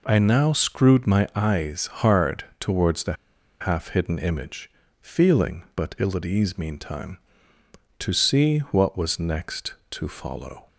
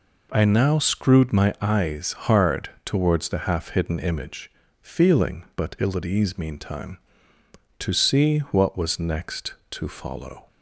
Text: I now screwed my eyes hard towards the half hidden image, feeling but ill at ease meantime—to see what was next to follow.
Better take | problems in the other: second | pauses between "hard" and "towards"; slight; at 2.4 s; 0.16 s long; slight in the second // pauses between "the" and "half"; noticeable; at 3.1 s; 0.47 s long

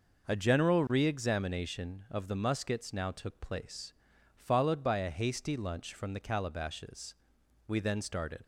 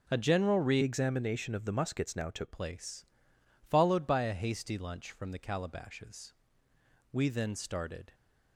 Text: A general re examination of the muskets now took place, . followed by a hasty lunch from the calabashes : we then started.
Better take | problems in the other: first | changes voice from "examination" to "took"; from 0.8 to 2.5 s; 1.7 s long

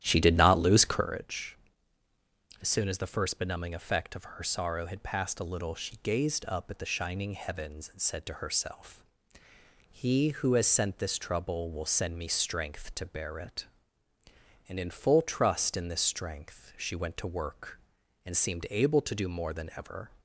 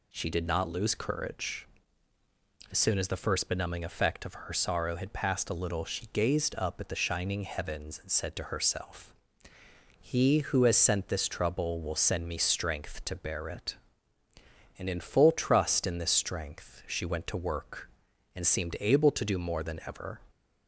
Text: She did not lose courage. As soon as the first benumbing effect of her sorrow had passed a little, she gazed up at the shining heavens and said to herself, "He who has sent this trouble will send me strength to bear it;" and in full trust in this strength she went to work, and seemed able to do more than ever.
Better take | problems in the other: second | starts louder than the rest; strong; until 1.2 s; 12 dB

